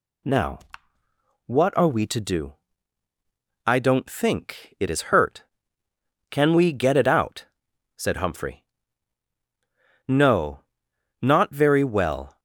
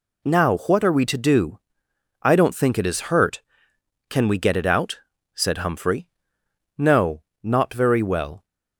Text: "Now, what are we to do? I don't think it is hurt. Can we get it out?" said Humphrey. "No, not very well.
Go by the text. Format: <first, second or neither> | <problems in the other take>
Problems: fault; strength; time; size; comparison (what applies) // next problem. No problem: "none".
neither | none